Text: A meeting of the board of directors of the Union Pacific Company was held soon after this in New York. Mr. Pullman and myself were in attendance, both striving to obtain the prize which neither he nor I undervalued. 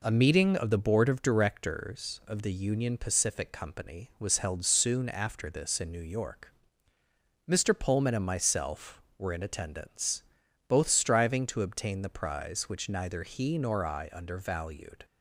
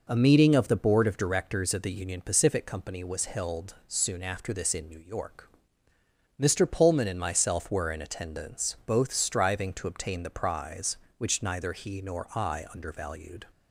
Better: neither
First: none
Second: none

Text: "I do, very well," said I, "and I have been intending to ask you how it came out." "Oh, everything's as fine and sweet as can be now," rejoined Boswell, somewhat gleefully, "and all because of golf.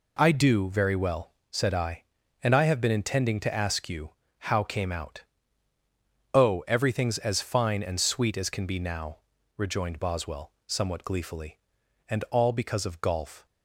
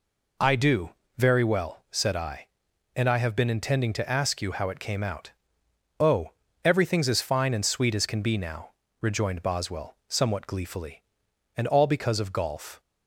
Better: second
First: pauses between "you" and "how"; slight; at 4.0 s; 0.30 s long // skips "it"; at 4.6 s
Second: none

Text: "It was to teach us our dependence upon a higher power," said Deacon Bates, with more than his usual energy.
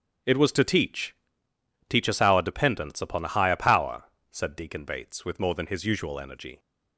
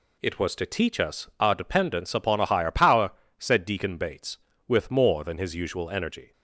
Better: second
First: starts louder than the rest; strong; until 2.0 s; 8.5 dB // says "teach" twice; at 1.8 s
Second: none

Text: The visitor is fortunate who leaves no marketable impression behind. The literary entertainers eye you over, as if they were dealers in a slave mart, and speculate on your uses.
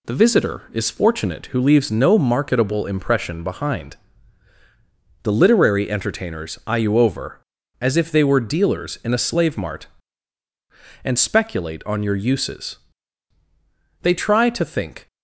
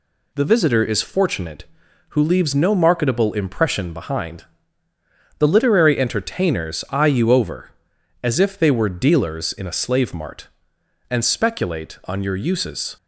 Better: second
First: goes on to say "They try to think"; noticeable; from 14.0 s on; 1.0 s long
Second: none

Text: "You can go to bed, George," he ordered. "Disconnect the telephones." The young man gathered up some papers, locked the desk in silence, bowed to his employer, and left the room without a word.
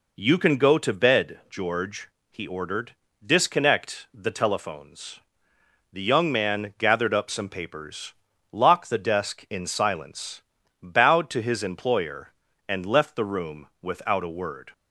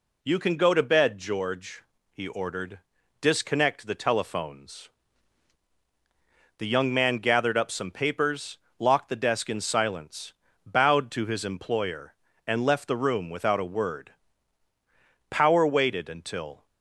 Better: first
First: none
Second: goes on to say "Power waited until"; from 15.3 s on; 1.3 s long

